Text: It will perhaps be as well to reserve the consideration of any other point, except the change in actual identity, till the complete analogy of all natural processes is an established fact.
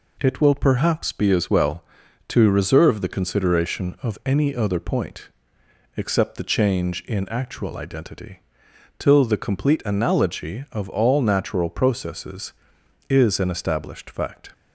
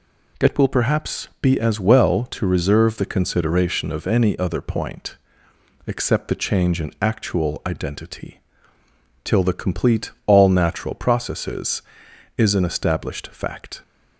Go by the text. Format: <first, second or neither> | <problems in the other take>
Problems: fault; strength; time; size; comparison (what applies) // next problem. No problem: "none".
first | skips "analogy of"; at 10.1 s